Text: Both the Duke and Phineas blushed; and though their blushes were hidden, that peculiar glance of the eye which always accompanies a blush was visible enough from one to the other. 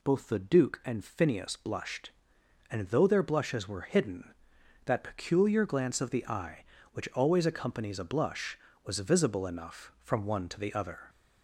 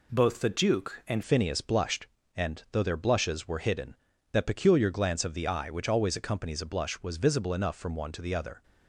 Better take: first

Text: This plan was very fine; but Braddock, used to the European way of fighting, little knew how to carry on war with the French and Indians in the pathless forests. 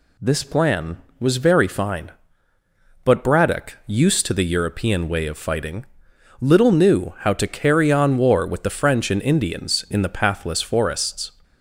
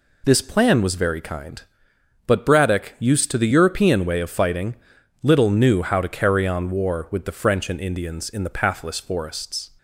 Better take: first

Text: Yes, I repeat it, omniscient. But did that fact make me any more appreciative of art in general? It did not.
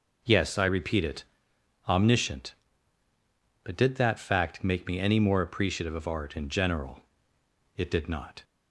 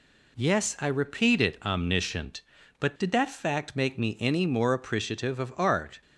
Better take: first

